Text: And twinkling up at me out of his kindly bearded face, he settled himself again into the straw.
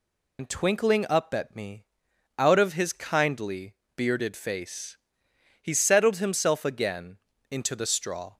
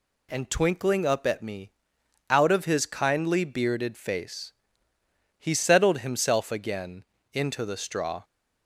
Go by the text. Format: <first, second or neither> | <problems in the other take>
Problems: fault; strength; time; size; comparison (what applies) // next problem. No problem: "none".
second | loses the start of "And"; at 0.3 s; 85 ms // pauses between "me" and "out"; noticeable; at 1.8 s; 0.52 s long; noticeable in the second // pauses between "kindly" and "bearded"; slight; at 3.7 s; 0.20 s long // pauses between "again" and "into"; slight; at 7.1 s; 0.32 s long; slight in the second